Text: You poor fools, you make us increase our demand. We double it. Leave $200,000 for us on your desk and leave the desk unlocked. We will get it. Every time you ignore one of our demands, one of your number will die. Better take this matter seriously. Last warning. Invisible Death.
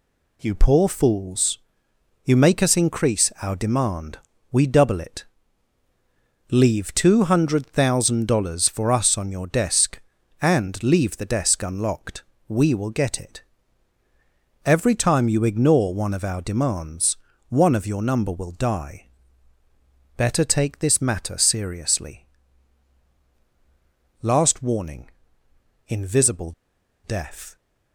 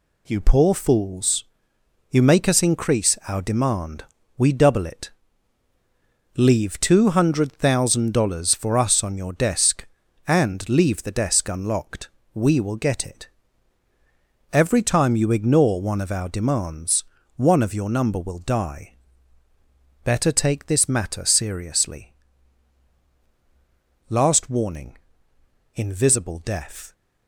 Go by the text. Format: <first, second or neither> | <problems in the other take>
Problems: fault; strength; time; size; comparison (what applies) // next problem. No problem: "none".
second | pauses between "Invisible" and "Death"; noticeable; at 26.5 s; 0.52 s long